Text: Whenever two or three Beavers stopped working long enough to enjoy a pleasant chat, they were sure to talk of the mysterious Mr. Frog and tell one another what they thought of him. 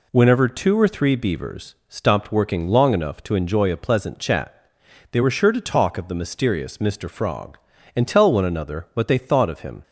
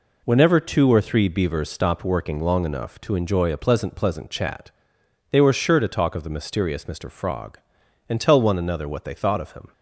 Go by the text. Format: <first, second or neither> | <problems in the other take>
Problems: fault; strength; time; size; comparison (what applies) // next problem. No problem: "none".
first | says "pleasant" twice; at 3.9 s